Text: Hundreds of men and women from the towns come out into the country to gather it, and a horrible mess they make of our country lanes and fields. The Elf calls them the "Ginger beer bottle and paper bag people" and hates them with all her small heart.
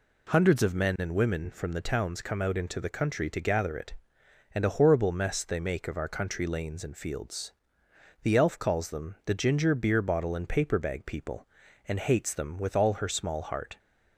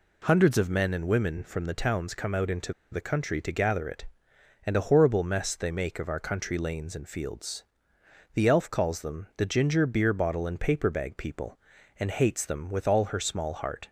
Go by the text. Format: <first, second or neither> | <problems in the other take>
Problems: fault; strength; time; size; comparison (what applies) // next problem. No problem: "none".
first | pauses between "into" and "the"; slight; at 2.7 s; 0.18 s long